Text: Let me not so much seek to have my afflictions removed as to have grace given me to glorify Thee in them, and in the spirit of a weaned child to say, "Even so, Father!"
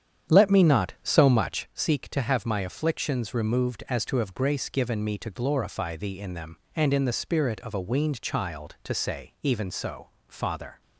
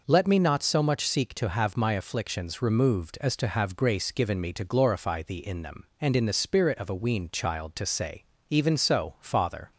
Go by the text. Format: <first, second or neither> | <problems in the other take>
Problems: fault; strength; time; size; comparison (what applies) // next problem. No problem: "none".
second | starts louder than the rest; strong; until 1.9 s; 9 dB